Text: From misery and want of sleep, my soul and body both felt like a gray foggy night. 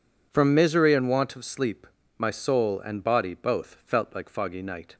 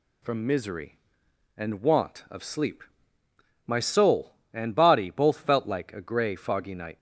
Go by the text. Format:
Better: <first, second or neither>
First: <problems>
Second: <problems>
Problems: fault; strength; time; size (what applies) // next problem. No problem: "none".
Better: second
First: skips "a gray"; at 4.2 s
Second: none